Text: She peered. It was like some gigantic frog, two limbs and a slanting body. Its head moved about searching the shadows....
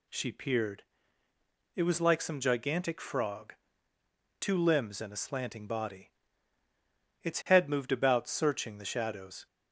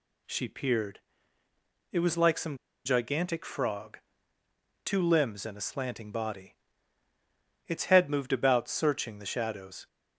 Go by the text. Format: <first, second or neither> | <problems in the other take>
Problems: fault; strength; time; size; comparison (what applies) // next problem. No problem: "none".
first | pauses between "some" and "gigantic"; slight; at 2.5 s; 0.28 s long